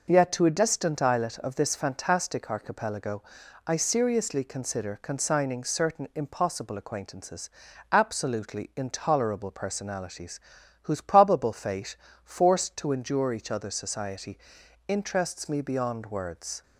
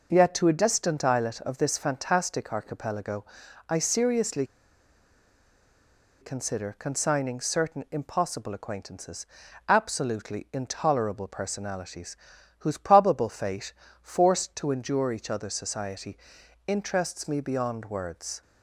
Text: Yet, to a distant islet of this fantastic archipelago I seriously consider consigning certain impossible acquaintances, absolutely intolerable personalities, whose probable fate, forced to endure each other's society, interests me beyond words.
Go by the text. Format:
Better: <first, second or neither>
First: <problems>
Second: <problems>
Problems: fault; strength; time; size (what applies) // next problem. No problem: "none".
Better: first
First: pauses between "archipelago" and "I"; noticeable; at 3.2 s; 0.46 s long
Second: pauses between "archipelago" and "I"; noticeable; at 3.2 s; 0.46 s long // pauses between "seriously" and "consider"; strong; at 4.4 s; 1.7 s long